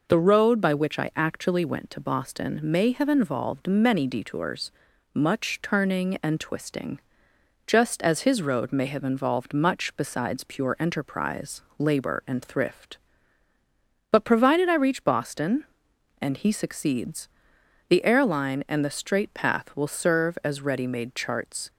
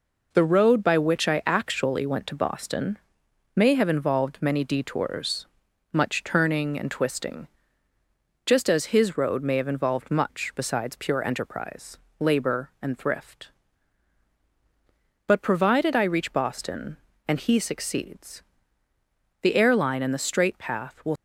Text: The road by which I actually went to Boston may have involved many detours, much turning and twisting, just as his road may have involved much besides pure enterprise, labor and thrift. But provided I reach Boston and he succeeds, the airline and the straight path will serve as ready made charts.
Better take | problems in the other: first | pauses between "Boston" and "may"; noticeable; at 2.9 s; 0.58 s long // stops before "serve as ready made charts"; at 21.1 s

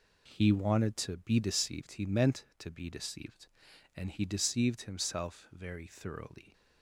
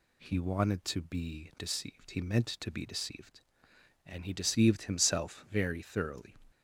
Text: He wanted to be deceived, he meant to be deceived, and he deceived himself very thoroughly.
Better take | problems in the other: neither | none

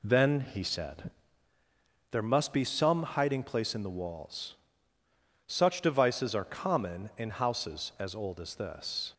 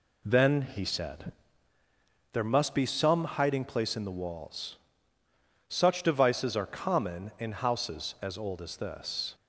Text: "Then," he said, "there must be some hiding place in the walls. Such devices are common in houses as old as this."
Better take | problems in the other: neither | none

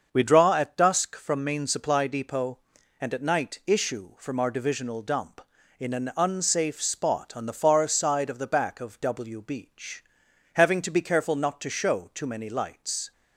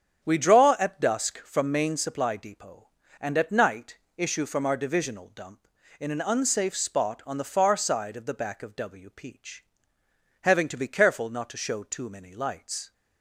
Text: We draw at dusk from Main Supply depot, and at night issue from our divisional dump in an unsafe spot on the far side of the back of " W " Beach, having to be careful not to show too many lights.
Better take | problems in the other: first | starts louder than the rest; strong; until 1.2 s; 8 dB; also in the first // pauses between "night" and "issue"; slight; at 3.9 s; 0.20 s long // says "Peach" for "Beach"; at 9.1 s

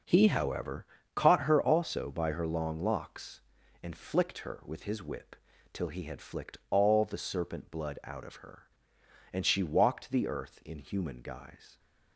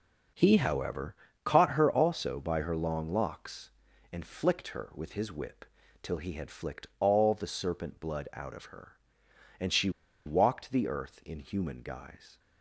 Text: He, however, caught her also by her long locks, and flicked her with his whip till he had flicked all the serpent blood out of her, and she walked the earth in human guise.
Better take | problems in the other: first | pauses between "whip" and "till"; slight; at 5.6 s; 0.36 s long; slight in the first // pauses between "she" and "walked"; at 9.8 s; 0.36 s long

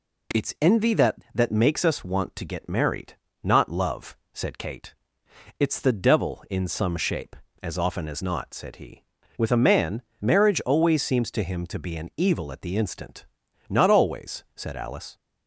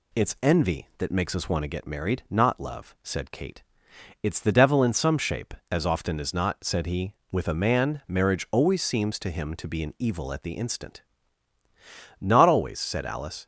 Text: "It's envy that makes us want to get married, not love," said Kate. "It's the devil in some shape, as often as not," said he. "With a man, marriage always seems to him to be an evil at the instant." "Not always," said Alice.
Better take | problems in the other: second | says "that" twice; at 1.3 s

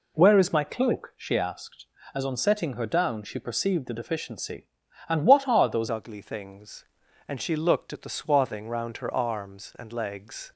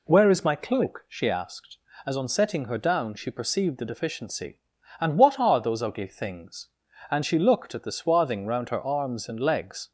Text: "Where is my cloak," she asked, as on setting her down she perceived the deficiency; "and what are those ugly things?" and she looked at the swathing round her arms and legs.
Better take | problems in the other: second | changes voice at "ugly"; from 5.8 s on; 4.7 s long

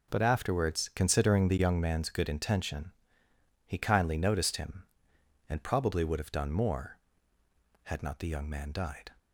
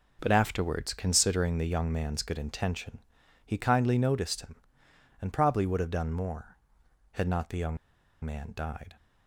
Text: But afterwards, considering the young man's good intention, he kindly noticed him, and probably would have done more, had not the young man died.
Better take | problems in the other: first | pauses between "young" and "man"; noticeable; at 7.7 s; 0.47 s long

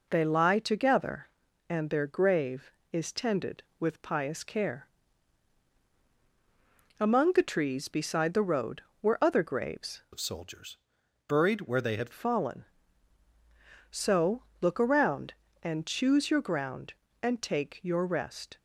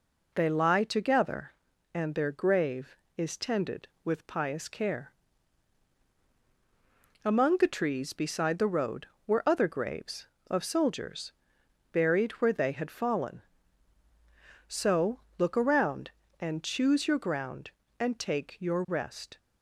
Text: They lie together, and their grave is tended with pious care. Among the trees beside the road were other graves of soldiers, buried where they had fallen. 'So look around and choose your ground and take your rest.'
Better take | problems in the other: second | changes voice from "of" to "had"; from 10.1 to 12.1 s; 2.0 s long // pauses between "So" and "look"; slight; at 14.4 s; 0.18 s long; slight in the second

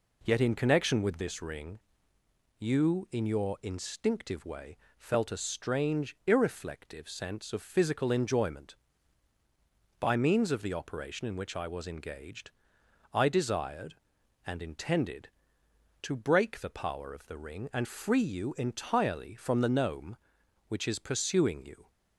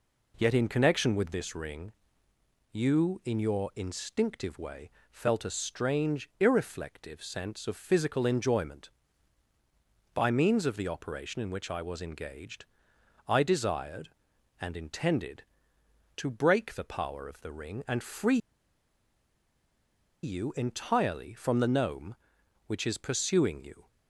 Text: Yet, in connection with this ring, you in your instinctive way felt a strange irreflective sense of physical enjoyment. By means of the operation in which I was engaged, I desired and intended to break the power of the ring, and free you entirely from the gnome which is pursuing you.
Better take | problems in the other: first | pauses between "way" and "felt"; slight; at 4.8 s; 0.20 s long; slight in the first // pauses between "free" and "you"; strong; at 18.3 s; 1.8 s long

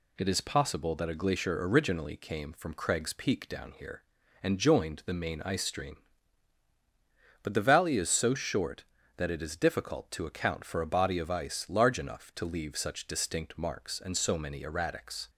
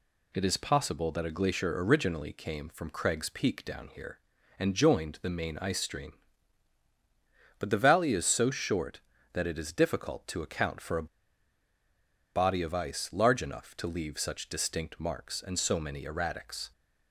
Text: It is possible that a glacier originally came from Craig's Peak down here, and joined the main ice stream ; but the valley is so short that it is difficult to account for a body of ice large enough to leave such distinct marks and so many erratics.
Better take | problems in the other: first | pauses between "a" and "body"; strong; at 11.0 s; 1.2 s long

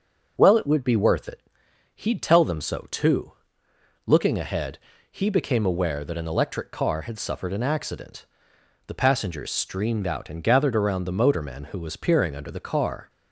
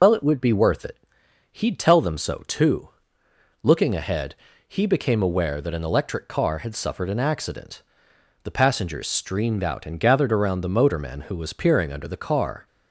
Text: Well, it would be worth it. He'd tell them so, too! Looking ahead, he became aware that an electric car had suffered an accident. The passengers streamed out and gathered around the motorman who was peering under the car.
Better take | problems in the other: first | loses the start of "Well"; at 0.0 s; 80 ms

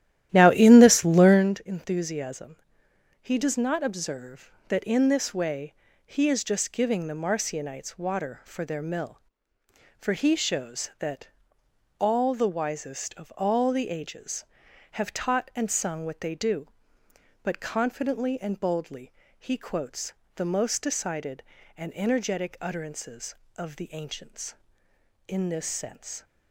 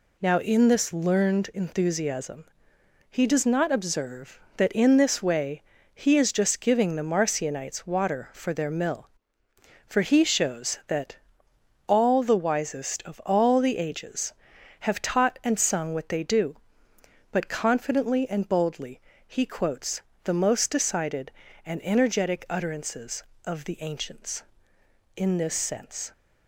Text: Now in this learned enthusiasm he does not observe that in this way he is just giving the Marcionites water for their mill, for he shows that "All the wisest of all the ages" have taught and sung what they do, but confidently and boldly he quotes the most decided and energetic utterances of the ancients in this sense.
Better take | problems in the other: second | starts louder than the rest; strong; until 1.6 s; 12.5 dB // pauses between "enthusiasm" and "he"; noticeable; at 2.5 s; 0.64 s long; noticeable in the second // pauses between "way" and "he"; slight; at 5.7 s; 0.32 s long; slight in the second // pauses between "that" and "All"; noticeable; at 11.2 s; 0.68 s long; noticeable in the second // pauses between "boldly" and "he"; slight; at 19.1 s; 0.24 s long; slight in the second // pauses between "quotes" and "the"; slight; at 20.1 s; 0.22 s long; slight in the second

